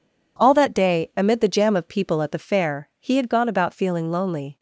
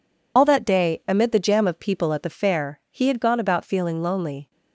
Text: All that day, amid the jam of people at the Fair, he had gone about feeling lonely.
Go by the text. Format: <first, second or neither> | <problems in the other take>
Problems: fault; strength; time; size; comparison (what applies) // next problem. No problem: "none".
first | loses the start of "All"; at 0.3 s; 85 ms